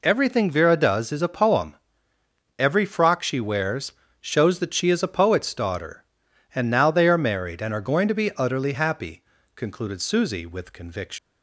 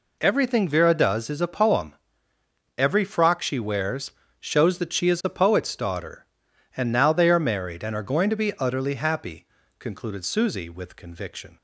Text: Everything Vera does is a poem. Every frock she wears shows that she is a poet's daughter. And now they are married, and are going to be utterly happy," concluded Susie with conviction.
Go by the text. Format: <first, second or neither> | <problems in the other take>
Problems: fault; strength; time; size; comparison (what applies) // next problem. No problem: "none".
second | pauses between "wears" and "shows"; slight; at 3.9 s; 0.30 s long; slight in the second // leaves "conviction" unfinished; at 11.1 s; 145 ms